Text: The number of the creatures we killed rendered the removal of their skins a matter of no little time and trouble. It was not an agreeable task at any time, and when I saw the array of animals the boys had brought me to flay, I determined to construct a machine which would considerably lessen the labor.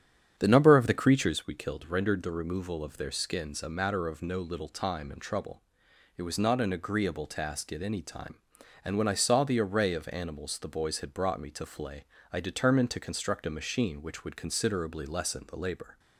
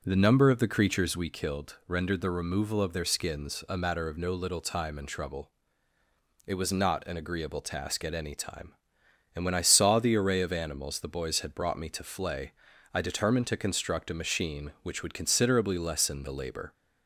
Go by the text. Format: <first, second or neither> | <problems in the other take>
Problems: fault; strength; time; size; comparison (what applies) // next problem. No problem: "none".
second | starts louder than the rest; strong; until 1.5 s; 8.5 dB